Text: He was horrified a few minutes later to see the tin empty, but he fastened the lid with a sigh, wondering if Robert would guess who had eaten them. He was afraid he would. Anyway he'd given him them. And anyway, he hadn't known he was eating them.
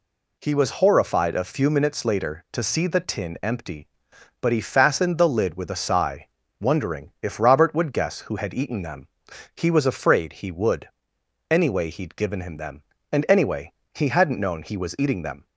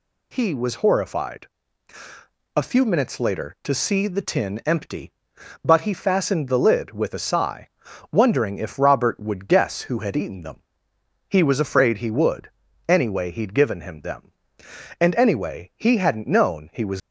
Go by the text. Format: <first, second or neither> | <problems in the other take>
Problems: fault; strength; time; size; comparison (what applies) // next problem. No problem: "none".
first | pauses between "horrified" and "a"; at 1.4 s; 1.1 s long // stops before "eating them"; at 16.9 s